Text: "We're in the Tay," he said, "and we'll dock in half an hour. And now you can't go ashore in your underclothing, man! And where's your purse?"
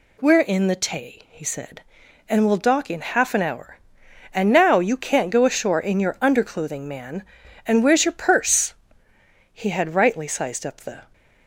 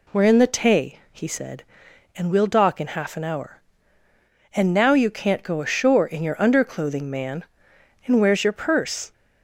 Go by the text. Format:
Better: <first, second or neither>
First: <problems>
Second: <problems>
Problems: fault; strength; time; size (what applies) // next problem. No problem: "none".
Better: second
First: goes on to say "He had rightly sized up the"; from 9.5 s on; 1.5 s long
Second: none